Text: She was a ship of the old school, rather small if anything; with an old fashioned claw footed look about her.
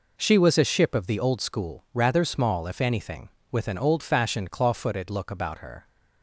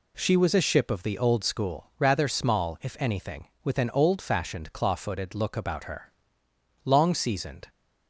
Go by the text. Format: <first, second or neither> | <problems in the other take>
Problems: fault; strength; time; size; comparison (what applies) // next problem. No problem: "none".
first | goes on to say "Long seasoned"; noticeable; from 6.8 s on; 0.82 s long